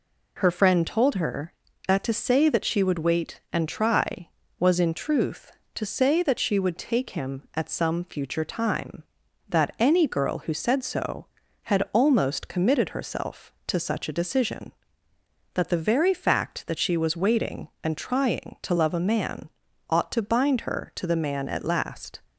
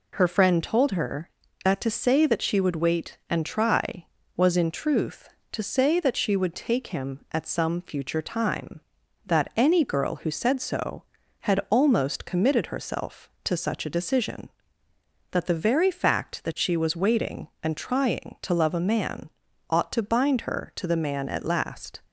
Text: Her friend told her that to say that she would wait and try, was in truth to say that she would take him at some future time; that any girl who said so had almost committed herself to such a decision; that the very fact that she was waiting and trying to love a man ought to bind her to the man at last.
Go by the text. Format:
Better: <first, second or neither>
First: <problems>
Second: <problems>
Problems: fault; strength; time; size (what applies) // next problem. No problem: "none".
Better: neither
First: pauses between "man" and "ought"; at 19.4 s; 0.40 s long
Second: pauses between "man" and "ought"; at 19.2 s; 0.40 s long